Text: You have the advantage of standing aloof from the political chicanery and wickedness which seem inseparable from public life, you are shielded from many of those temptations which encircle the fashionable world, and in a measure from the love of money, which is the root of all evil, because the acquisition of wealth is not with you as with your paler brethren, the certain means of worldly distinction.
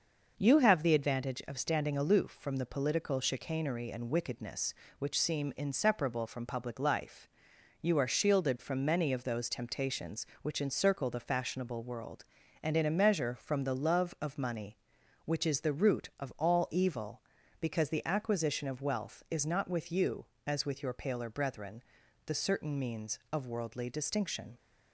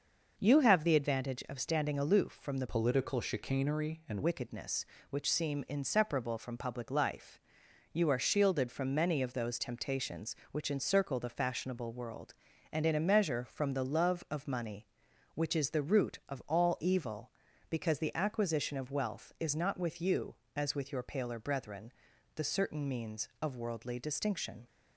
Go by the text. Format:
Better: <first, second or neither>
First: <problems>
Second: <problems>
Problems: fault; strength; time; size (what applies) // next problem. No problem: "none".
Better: first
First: none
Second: changes voice from "political" to "and"; from 2.6 to 4.2 s; 1.6 s long